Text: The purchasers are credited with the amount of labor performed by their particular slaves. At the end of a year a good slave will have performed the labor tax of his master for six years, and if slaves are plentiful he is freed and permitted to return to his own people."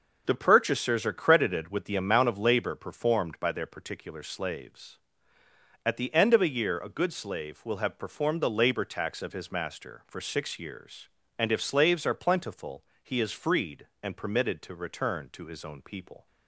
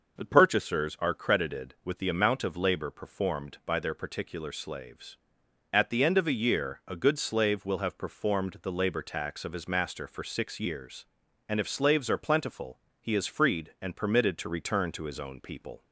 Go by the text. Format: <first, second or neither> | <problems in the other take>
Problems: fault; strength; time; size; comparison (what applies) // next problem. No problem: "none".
neither | pauses between "plentiful" and "he"; slight; the same in both